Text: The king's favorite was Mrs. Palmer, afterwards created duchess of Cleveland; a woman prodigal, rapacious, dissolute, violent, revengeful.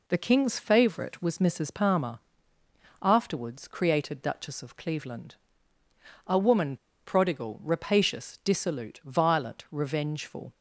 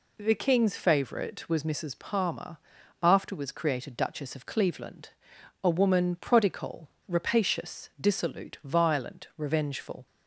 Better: second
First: pauses between "woman" and "prodigal"; slight; at 6.7 s; 0.30 s long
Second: none

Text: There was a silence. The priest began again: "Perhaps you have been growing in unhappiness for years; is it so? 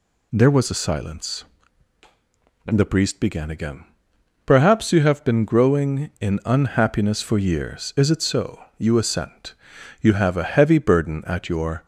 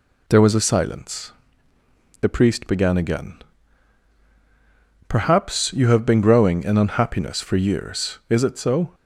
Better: second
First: goes on to say "you assent You have a heavy burden at your"; strong; from 8.7 s on; 3.0 s long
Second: none

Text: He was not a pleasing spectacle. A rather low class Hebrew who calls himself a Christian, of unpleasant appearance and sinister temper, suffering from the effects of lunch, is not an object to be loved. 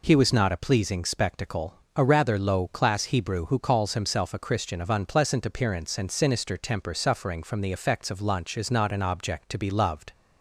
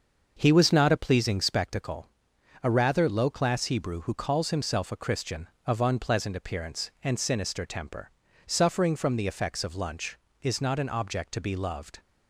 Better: first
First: none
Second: starts louder than the rest; until 1.7 s; 6.5 dB

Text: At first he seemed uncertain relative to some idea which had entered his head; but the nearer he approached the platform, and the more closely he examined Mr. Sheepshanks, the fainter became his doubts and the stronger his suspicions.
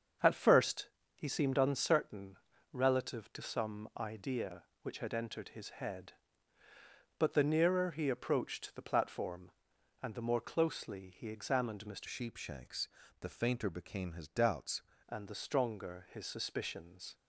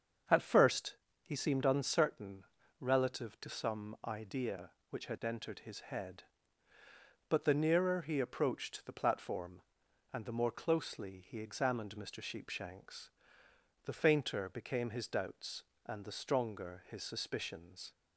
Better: second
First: starts louder than the rest; until 1.4 s; 7 dB // pauses between "first" and "he"; slight; at 0.8 s; 0.26 s long // pauses between "uncertain" and "relative"; slight; at 2.3 s; 0.36 s long // changes voice from "Sheepshanks" to "doubts"; from 12.0 to 14.8 s; 2.8 s long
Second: starts louder than the rest; until 1.5 s; 7 dB // pauses between "first" and "he"; slight; at 0.9 s; 0.26 s long // pauses between "uncertain" and "relative"; slight; at 2.4 s; 0.36 s long

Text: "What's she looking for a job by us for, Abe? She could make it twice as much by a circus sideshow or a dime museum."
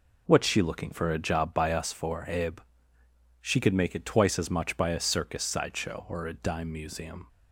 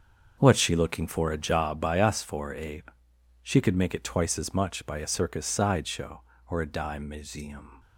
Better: first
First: none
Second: gets quieter; strong; throughout; 11.5 dB

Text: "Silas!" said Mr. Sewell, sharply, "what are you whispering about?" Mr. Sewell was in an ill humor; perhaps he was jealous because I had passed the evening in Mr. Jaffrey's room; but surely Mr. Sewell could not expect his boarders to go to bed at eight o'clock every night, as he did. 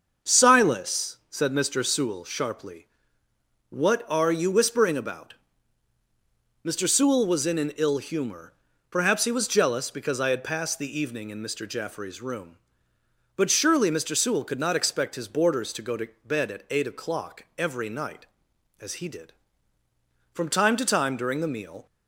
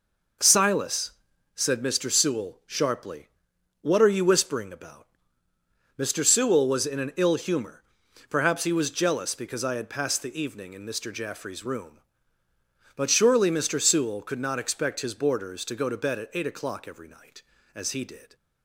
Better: second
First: starts louder than the rest; until 1.3 s; 6.5 dB // pauses between "to" and "bed"; slight; at 16.0 s; 0.16 s long // goes on to say "From time to time during the meal"; from 20.3 s on; 1.5 s long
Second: none

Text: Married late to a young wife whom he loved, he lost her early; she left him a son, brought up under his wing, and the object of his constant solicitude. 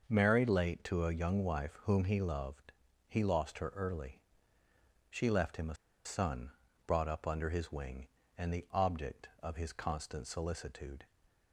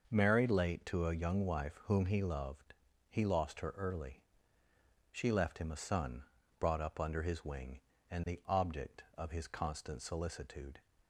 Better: second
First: starts louder than the rest; noticeable; until 1.0 s; 6 dB // pauses between "a" and "son"; slight; at 5.7 s; 0.30 s long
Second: starts louder than the rest; noticeable; until 1.1 s; 6 dB

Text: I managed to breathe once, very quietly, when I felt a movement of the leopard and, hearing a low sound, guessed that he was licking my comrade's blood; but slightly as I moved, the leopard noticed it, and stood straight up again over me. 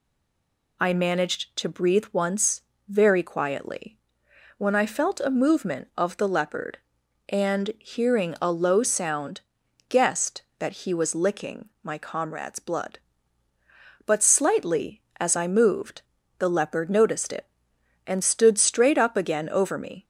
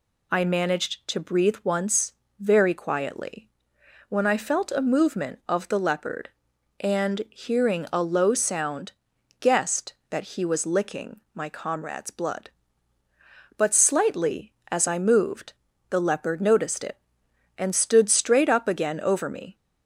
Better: second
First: stays silent before the first word; slight; until 0.8 s; 0.8 s long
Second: none

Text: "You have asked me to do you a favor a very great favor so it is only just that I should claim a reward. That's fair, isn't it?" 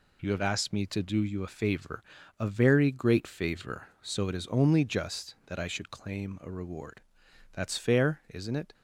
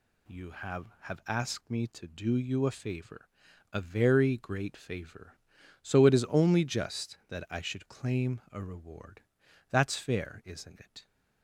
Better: first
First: pauses between "favor" and "a"; at 2.0 s; 0.38 s long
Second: says "have" twice; at 1.0 s // pauses between "favor" and "a"; at 3.2 s; 0.44 s long

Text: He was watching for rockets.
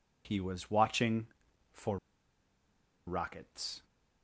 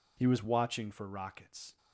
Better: second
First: pauses between "for" and "rockets"; at 1.9 s; 1.1 s long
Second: none

